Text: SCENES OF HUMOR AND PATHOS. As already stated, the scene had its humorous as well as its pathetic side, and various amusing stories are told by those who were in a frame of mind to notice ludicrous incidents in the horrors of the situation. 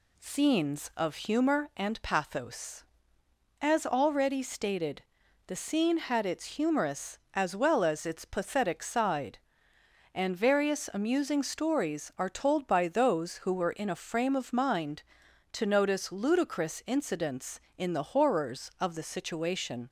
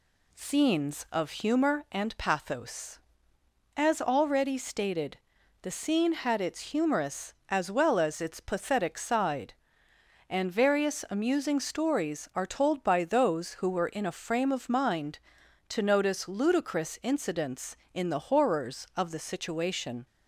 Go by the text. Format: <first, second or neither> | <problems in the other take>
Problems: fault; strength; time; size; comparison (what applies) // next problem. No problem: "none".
neither | none